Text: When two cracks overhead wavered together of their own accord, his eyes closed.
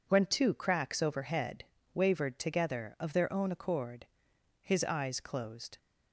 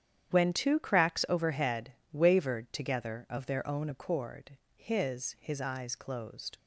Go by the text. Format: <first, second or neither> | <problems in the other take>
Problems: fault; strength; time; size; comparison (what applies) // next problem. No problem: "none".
first | starts louder than the rest; strong; until 1.3 s; 9.5 dB // pauses between "overhead" and "wavered"; slight; at 1.9 s; 0.20 s long; slight in the first // says "his" twice; at 5.3 s